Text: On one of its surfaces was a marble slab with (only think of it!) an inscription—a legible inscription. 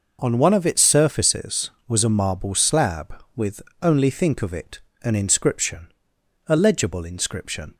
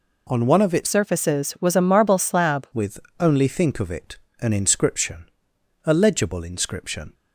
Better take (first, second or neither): first